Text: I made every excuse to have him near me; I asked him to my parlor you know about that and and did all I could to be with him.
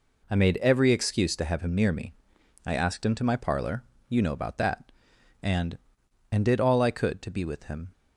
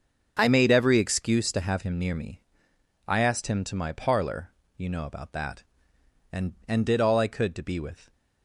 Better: first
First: pauses between "parlor" and "you"; slight; at 3.8 s; 0.26 s long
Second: starts louder than the rest; until 1.4 s; 6 dB // pauses between "parlor" and "you"; slight; at 4.5 s; 0.24 s long // stops before "him"; at 8.1 s

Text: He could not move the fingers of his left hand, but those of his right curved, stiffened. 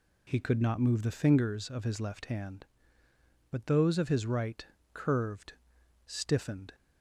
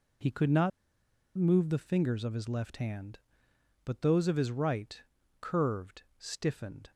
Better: first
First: pauses between "right" and "curved"; slight; at 4.6 s; 0.25 s long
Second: pauses between "not" and "move"; noticeable; at 0.7 s; 0.66 s long // pauses between "right" and "curved"; at 5.0 s; 0.38 s long

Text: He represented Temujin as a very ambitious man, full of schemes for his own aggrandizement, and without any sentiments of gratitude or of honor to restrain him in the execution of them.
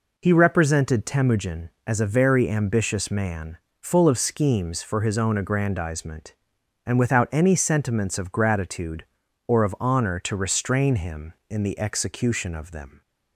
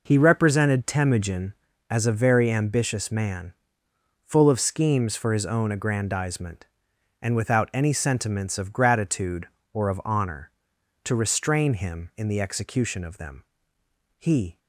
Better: first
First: none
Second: goes on to say "He"; slight; from 14.1 s on; 0.42 s long

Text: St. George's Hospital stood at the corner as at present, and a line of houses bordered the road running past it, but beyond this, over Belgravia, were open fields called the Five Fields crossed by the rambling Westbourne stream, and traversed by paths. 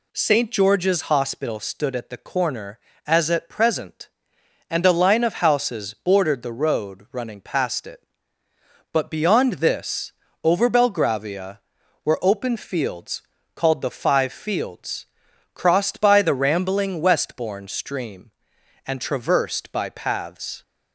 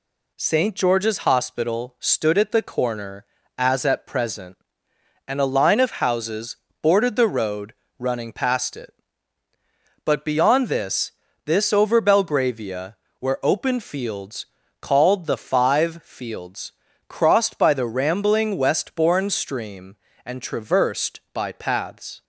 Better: first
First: pauses between "fields" and "called"; slight; at 13.2 s; 0.32 s long // pauses between "Fields" and "crossed"; noticeable; at 15.0 s; 0.48 s long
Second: pauses between "houses" and "bordered"; slight; at 6.5 s; 0.26 s long // pauses between "road" and "running"; slight; at 7.7 s; 0.26 s long // says "this" twice; at 11.4 s // pauses between "fields" and "called"; slight; at 14.4 s; 0.36 s long // pauses between "Fields" and "crossed"; at 16.7 s; 0.38 s long

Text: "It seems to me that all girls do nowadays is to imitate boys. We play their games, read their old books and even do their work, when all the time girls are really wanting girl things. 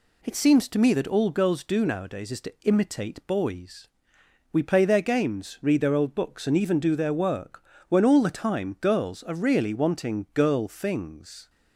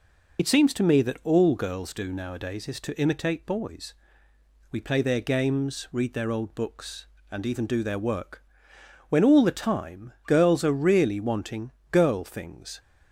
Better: first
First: none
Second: loses the start of "It"; at 0.3 s; 35 ms // pauses between "wanting" and "girl"; slight; at 11.6 s; 0.22 s long

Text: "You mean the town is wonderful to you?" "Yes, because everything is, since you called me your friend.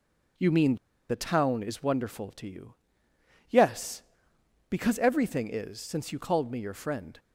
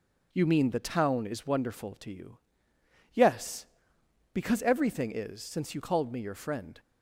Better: second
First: pauses between "mean" and "the"; slight; at 0.7 s; 0.33 s long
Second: none

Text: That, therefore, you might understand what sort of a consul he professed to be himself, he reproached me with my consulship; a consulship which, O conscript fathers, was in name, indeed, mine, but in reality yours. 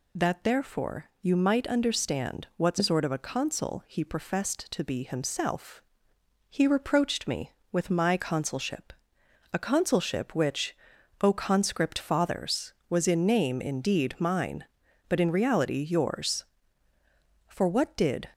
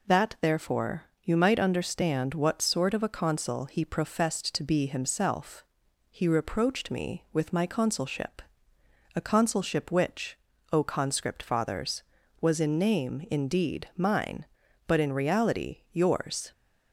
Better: second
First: goes on to say "For what did"; noticeable; from 17.4 s on; 0.84 s long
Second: none

